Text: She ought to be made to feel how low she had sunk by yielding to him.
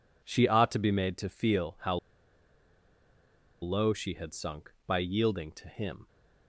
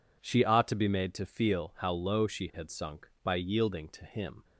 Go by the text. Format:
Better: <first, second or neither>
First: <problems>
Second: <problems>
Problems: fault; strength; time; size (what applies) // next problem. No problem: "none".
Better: second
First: pauses between "how" and "low"; strong; at 1.9 s; 1.6 s long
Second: none